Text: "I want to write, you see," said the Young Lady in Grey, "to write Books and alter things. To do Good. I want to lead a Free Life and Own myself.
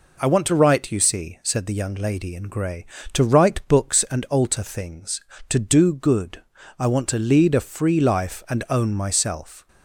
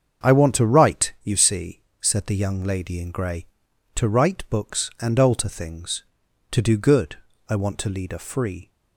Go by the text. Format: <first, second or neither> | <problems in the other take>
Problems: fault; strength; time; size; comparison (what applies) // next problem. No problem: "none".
first | starts louder than the rest; until 1.3 s; 7 dB // stops before "Life and Own myself"; at 8.6 s